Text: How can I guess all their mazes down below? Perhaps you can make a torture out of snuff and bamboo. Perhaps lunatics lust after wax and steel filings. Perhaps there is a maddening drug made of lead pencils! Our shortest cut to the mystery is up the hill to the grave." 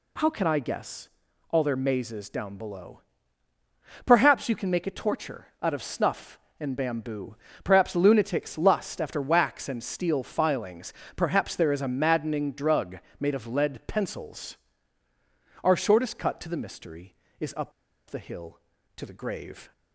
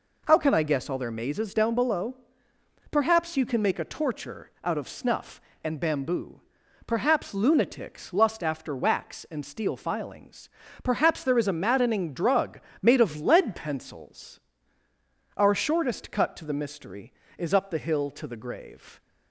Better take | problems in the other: second | pauses between "guess" and "all"; at 1.0 s; 0.42 s long // pauses between "drug" and "made"; slight; at 12.9 s; 0.24 s long; slight in the second // pauses between "up" and "the"; at 17.7 s; 0.38 s long

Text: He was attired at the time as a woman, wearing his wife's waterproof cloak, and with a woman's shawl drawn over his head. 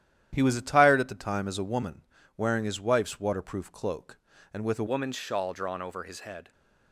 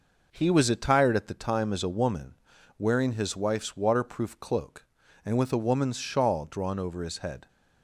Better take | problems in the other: second | starts louder than the rest; strong; until 1.3 s; 11 dB // changes voice at "woman's"; from 4.8 s on; 1.7 s long

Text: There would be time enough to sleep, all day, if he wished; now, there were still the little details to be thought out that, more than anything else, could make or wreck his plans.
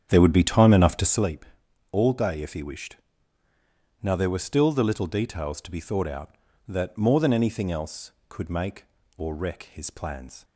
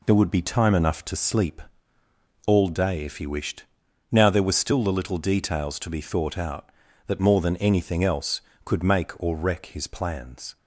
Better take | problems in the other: second | starts louder than the rest; strong; until 1.3 s; 8.5 dB

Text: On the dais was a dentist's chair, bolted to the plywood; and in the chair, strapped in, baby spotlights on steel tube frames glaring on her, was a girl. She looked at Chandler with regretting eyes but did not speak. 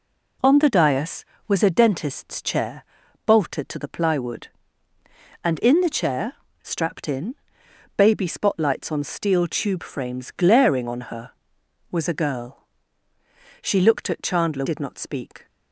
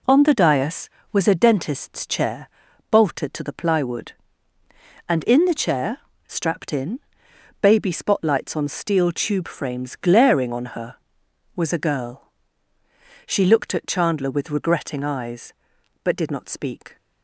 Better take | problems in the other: second | skips "with regretting eyes but"; at 14.6 s

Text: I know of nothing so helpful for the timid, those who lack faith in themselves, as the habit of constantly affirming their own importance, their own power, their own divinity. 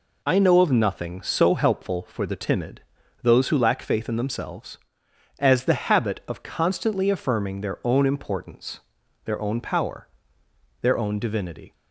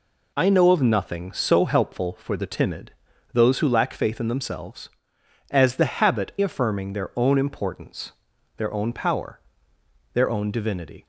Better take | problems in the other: first | skips "of constantly"; at 6.3 s

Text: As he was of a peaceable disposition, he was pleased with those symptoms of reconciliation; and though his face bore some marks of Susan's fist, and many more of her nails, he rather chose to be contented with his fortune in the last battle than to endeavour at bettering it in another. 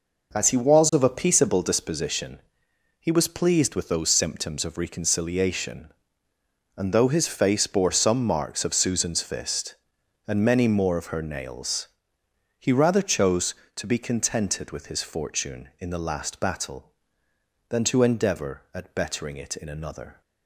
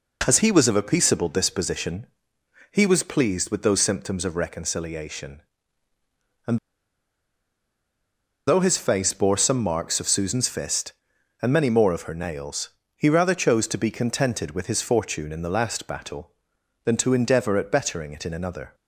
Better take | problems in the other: first | pauses between "and" and "though"; strong; at 6.5 s; 1.9 s long

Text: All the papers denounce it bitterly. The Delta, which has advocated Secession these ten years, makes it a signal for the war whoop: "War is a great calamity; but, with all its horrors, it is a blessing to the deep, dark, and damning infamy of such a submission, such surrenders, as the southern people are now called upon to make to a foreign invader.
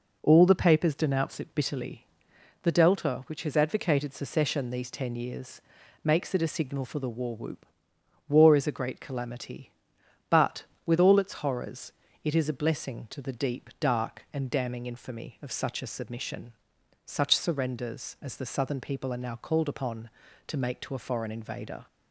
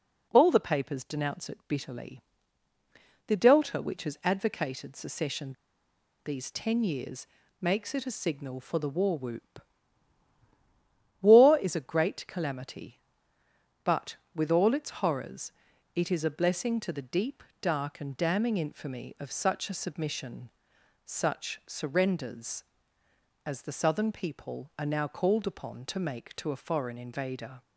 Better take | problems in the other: first | pauses between "Secession" and "these"; noticeable; at 5.5 s; 0.73 s long

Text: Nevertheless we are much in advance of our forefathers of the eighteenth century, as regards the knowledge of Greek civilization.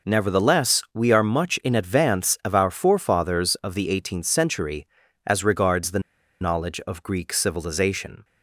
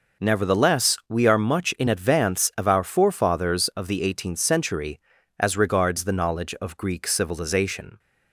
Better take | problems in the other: second | pauses between "the" and "knowledge"; at 5.9 s; 0.41 s long

